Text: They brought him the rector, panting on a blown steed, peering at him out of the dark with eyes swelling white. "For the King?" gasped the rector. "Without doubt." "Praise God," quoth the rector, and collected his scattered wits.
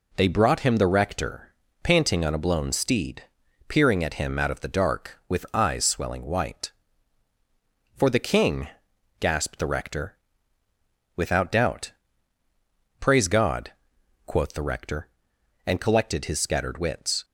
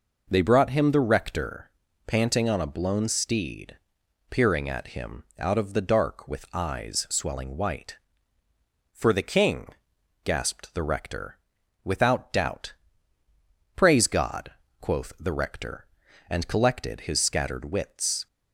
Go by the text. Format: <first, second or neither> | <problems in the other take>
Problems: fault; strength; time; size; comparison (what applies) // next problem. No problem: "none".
neither | none